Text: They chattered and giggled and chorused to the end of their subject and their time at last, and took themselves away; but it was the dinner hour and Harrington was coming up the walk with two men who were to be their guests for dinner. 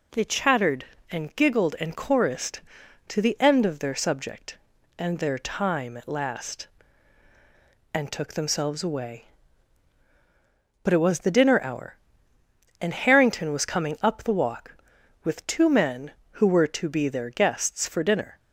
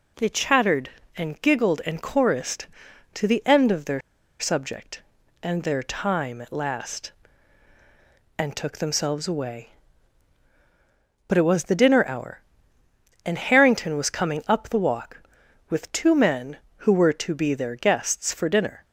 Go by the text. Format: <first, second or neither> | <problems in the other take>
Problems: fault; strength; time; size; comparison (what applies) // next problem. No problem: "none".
first | pauses between "their" and "subject"; at 4.0 s; 0.39 s long